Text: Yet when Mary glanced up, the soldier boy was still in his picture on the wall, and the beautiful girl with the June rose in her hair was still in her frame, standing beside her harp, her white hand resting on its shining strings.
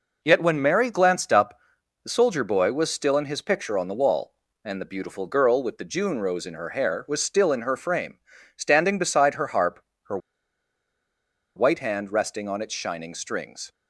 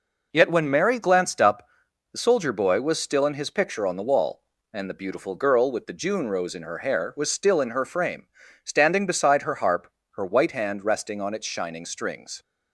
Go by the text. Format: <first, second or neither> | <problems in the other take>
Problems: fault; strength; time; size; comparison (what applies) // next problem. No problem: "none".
second | pauses between "her" and "white"; strong; at 10.1 s; 1.3 s long